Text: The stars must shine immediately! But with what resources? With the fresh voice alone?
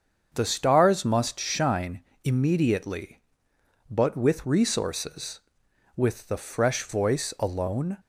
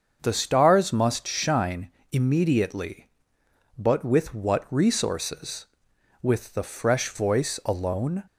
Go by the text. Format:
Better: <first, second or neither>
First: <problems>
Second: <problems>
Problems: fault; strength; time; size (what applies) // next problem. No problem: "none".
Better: second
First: starts louder than the rest; until 1.3 s; 6.5 dB // pauses between "shine" and "immediately"; slight; at 2.0 s; 0.20 s long // skips "what"; at 4.4 s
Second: starts louder than the rest; until 1.2 s; 6.5 dB // pauses between "shine" and "immediately"; slight; at 1.9 s; 0.20 s long